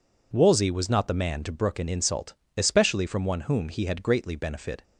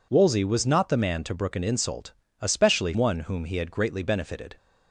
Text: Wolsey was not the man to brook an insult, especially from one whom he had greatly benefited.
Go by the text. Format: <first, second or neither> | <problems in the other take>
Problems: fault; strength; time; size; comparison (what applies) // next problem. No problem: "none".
first | skips "from"; at 2.9 s